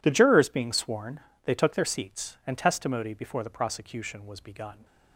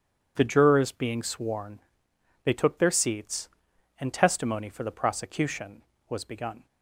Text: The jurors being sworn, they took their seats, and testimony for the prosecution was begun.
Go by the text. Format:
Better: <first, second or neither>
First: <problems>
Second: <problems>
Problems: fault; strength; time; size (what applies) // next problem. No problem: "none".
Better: second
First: says "before" for "for"; at 3.1 s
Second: none